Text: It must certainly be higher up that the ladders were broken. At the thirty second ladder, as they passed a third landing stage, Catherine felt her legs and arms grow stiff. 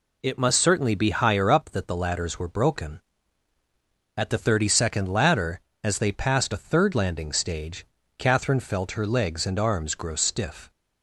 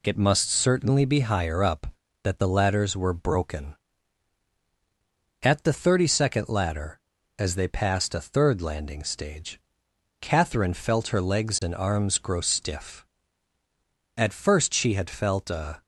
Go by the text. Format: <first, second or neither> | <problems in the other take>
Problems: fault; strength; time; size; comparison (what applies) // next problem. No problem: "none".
first | goes on to say "At first she had felt a"; strong; from 14.1 s on; 1.6 s long